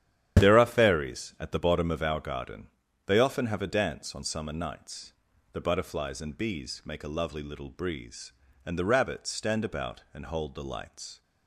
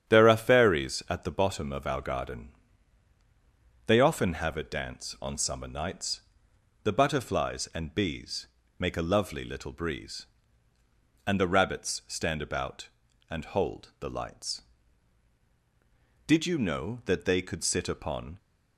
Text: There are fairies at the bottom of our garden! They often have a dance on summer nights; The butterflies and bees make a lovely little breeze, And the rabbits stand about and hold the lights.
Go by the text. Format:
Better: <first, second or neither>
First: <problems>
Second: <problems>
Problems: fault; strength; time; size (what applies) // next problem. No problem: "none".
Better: first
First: starts louder than the rest; strong; until 1.4 s; 10.5 dB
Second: starts louder than the rest; strong; until 1.1 s; 9 dB // pauses between "bees" and "make"; slight; at 8.4 s; 0.32 s long // goes on to say "Did you know that they could sit upon"; strong; from 16.2 s on; 2.1 s long